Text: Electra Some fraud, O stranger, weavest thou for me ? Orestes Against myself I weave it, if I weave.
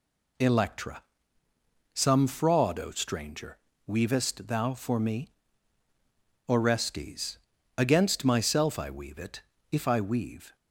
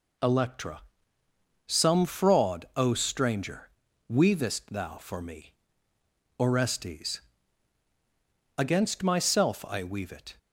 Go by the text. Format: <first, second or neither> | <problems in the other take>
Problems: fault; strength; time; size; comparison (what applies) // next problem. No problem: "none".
first | pauses between "Electra" and "Some"; noticeable; at 0.8 s; 0.86 s long; noticeable in the first // pauses between "Orestes" and "Against"; strong; at 7.1 s; 1.3 s long; also in the first // stops before "if I weave"; at 10.3 s